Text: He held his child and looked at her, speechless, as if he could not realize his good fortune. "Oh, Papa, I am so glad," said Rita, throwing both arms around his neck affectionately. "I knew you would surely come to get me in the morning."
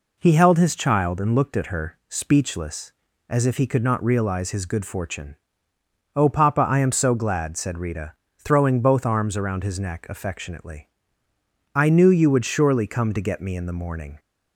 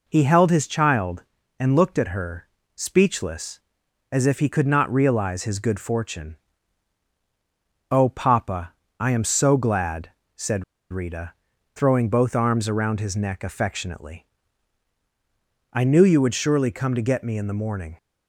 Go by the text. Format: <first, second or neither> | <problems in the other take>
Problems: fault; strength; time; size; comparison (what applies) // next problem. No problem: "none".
first | pauses between "said" and "Rita"; slight; at 10.6 s; 0.26 s long